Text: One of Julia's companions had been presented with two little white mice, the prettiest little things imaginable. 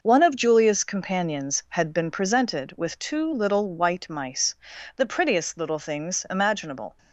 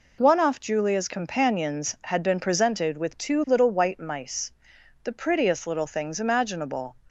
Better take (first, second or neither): first